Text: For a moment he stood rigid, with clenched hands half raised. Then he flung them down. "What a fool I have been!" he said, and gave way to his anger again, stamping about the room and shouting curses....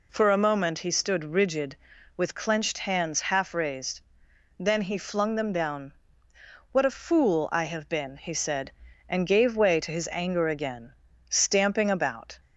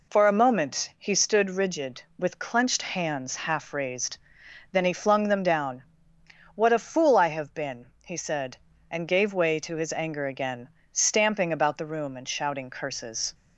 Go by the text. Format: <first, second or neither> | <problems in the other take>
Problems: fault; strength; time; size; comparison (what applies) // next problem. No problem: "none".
second | stops before "the room and shouting curses"; at 12.4 s